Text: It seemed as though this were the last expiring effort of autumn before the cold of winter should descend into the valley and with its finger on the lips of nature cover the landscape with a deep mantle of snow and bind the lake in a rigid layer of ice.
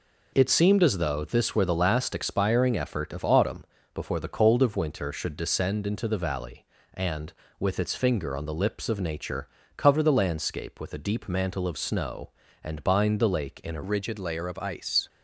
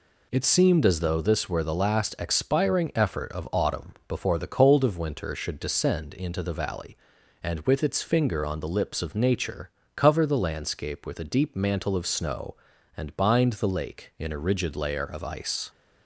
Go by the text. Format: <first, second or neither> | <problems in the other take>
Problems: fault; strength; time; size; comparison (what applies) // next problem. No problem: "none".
second | pauses between "autumn" and "before"; slight; at 3.6 s; 0.30 s long // pauses between "nature" and "cover"; slight; at 9.4 s; 0.28 s long; slight in the second // changes voice at "rigid"; from 13.8 s on; 1.2 s long